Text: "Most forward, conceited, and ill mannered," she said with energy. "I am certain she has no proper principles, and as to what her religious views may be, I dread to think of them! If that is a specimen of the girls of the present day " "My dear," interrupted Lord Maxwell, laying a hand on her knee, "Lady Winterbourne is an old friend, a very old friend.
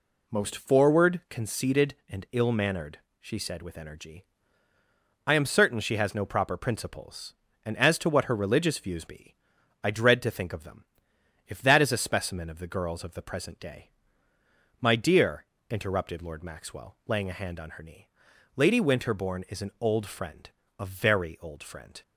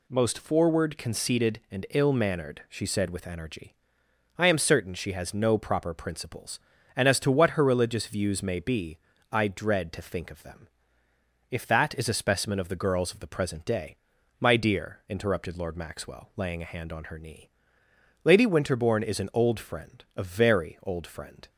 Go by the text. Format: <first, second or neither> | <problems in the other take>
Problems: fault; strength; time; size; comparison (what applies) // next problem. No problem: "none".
second | skips "may"; at 9.0 s